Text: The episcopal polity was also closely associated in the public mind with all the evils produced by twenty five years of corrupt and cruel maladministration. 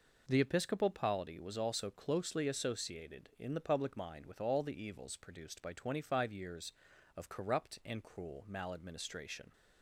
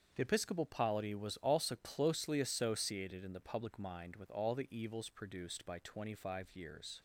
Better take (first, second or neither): first